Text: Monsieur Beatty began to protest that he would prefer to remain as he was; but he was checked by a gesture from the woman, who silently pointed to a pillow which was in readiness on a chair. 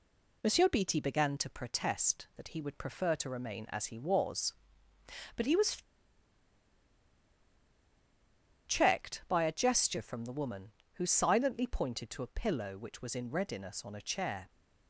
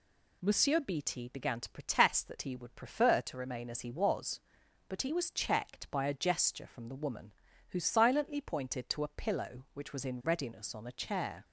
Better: second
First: pauses between "was" and "checked"; strong; at 5.7 s; 2.9 s long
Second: none

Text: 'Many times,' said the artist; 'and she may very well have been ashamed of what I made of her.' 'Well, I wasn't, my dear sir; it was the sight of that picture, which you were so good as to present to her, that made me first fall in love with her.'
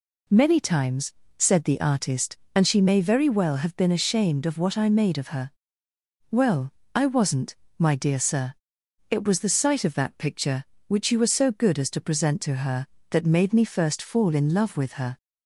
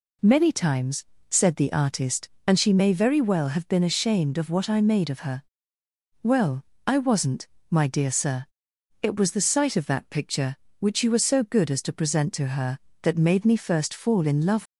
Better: first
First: none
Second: stops before "with her"; at 14.6 s

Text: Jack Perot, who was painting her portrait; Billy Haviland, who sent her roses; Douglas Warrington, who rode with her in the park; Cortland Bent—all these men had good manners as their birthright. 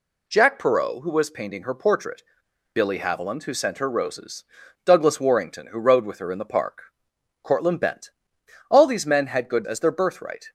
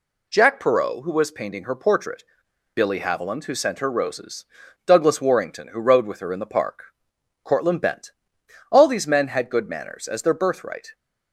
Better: second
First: skips "manners"; at 9.6 s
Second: none

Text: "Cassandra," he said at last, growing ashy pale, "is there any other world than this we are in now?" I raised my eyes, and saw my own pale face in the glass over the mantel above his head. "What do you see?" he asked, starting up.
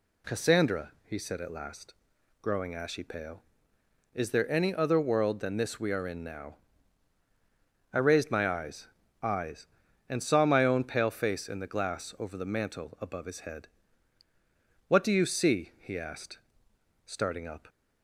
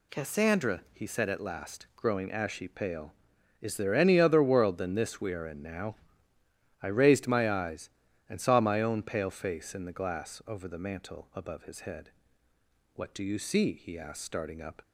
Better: second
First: says "eyes" twice; at 9.2 s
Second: none

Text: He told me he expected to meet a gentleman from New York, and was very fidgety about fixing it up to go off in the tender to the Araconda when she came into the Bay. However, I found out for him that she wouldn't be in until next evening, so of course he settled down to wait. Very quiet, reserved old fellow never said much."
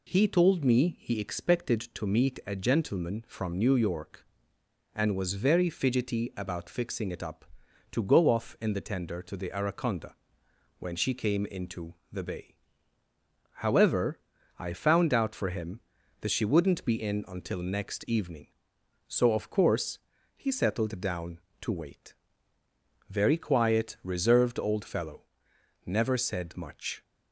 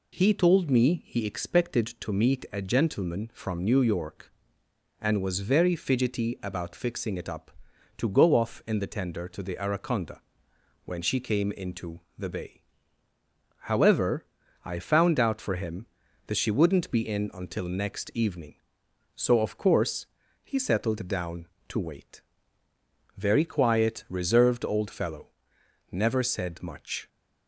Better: neither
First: pauses between "Araconda" and "when"; noticeable; at 10.1 s; 0.66 s long // pauses between "into" and "the"; slight; at 11.9 s; 0.16 s long // pauses between "course" and "he"; at 19.9 s; 0.38 s long // pauses between "fellow" and "never"; noticeable; at 25.2 s; 0.62 s long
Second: pauses between "Araconda" and "when"; noticeable; at 10.1 s; 0.66 s long // pauses between "into" and "the"; slight; at 11.9 s; 0.16 s long // pauses between "course" and "he"; at 20.0 s; 0.38 s long // pauses between "fellow" and "never"; noticeable; at 25.2 s; 0.62 s long

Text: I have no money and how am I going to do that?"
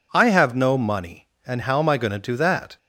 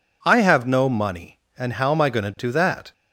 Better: neither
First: none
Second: none

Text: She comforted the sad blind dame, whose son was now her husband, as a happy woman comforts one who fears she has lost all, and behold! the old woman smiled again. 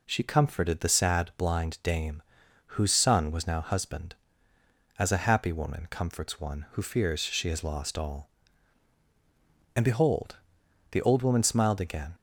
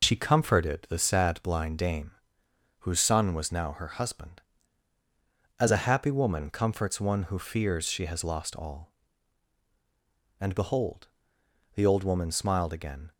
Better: second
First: skips "her"; at 3.6 s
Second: none

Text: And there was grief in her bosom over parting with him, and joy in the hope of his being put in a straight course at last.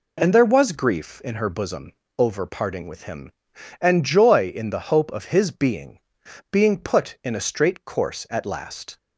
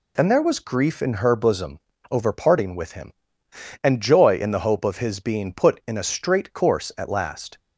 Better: second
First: pauses between "bosom" and "over"; slight; at 1.9 s; 0.24 s long // says "being" twice; at 6.5 s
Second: pauses between "bosom" and "over"; slight; at 1.7 s; 0.32 s long

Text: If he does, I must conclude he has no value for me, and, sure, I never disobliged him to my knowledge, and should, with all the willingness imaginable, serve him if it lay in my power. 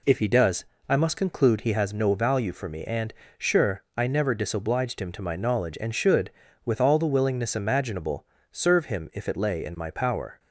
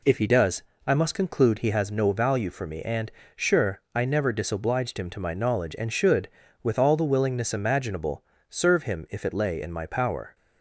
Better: neither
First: none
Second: none

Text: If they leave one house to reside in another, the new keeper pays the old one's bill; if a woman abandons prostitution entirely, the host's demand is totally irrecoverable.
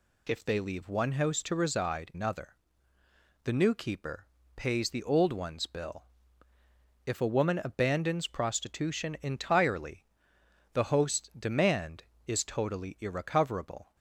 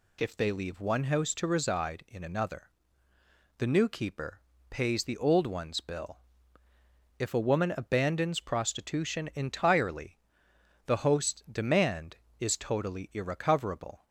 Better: second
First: skips "in"; at 2.1 s // pauses between "keeper" and "pays"; slight; at 4.2 s; 0.28 s long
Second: pauses between "keeper" and "pays"; slight; at 4.4 s; 0.28 s long

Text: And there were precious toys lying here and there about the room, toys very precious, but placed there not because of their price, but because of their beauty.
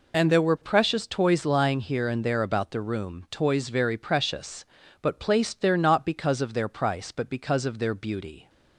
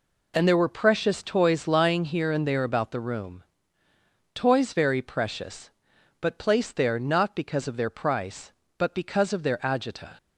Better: first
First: none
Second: says "agita" for "beauty"; at 9.5 s

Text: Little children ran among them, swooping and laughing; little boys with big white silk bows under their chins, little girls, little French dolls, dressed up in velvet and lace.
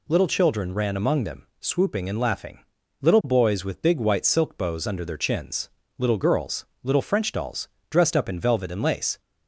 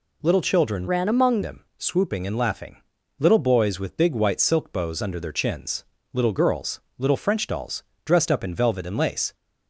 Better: first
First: none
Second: changes voice from "ran" to "among"; from 0.8 to 1.4 s; 0.6 s long

